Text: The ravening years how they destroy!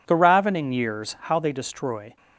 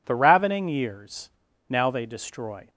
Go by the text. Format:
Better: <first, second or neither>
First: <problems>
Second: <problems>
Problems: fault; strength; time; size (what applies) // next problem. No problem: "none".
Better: first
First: none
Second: says "now" for "how"; at 1.6 s